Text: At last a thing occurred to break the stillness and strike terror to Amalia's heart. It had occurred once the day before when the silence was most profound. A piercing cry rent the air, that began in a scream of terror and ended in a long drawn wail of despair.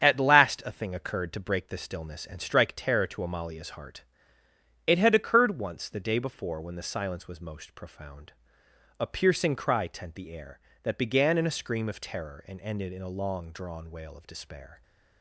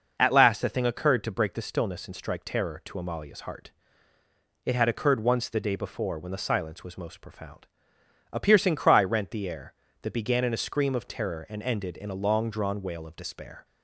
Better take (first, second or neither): second